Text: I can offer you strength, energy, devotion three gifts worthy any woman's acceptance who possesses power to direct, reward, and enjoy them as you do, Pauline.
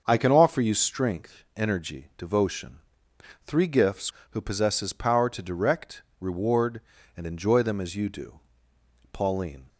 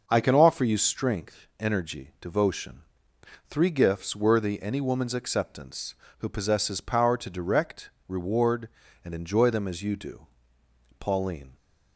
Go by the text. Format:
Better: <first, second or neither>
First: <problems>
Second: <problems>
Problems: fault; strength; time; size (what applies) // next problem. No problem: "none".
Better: second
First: starts louder than the rest; until 1.0 s; 6.5 dB // pauses between "devotion" and "three"; noticeable; at 2.7 s; 0.66 s long // skips "worthy any woman's acceptance"; at 4.2 s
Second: starts louder than the rest; noticeable; until 1.0 s; 6 dB // pauses between "devotion" and "three"; noticeable; at 2.8 s; 0.66 s long